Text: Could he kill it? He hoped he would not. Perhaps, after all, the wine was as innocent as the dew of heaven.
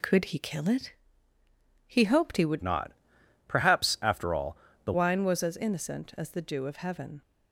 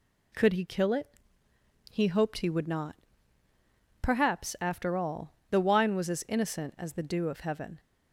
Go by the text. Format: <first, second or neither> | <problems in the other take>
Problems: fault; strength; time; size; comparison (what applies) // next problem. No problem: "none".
second | changes voice from "not" to "the"; from 2.6 to 4.9 s; 2.3 s long